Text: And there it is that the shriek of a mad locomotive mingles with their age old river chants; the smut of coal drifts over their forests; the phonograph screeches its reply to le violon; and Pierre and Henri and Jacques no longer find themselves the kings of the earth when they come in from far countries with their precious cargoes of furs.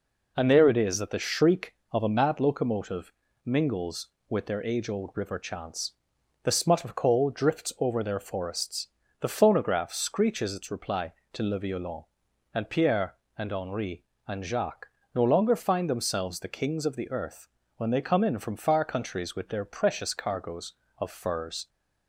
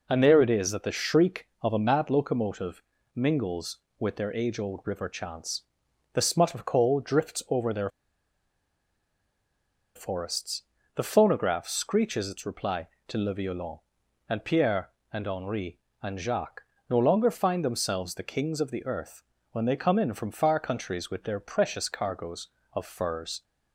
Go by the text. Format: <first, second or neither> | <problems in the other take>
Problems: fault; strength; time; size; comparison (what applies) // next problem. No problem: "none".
first | pauses between "locomotive" and "mingles"; slight; at 2.8 s; 0.34 s long; slight in the first // pauses between "their" and "forests"; strong; at 7.8 s; 2.0 s long // pauses between "Jacques" and "no"; slight; at 16.6 s; 0.26 s long; slight in the first // pauses between "earth" and "when"; slight; at 19.2 s; 0.28 s long; slight in the first